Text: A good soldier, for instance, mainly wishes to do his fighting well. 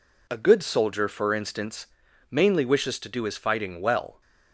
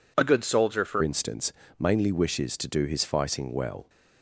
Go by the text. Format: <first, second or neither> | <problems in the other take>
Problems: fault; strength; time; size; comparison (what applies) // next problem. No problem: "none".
first | changes voice at "instance"; from 1.0 s on; 2.8 s long